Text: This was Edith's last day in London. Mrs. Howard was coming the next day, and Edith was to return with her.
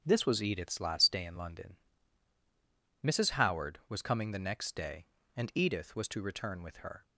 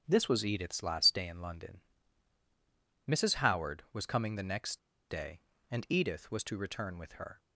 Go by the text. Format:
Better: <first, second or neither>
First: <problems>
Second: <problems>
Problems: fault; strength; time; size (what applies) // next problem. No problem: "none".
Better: first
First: starts louder than the rest; strong; until 1.0 s; 7 dB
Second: starts louder than the rest; strong; until 1.0 s; 7.5 dB // pauses between "next" and "day"; slight; at 4.7 s; 0.31 s long